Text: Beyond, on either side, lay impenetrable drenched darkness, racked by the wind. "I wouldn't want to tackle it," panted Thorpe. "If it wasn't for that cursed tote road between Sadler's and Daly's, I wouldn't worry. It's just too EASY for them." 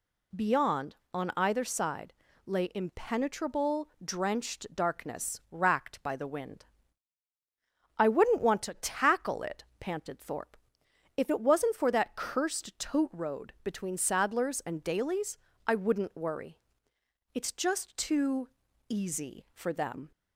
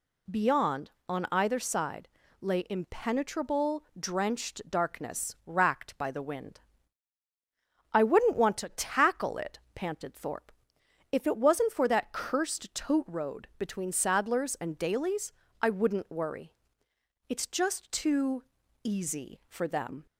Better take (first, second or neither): neither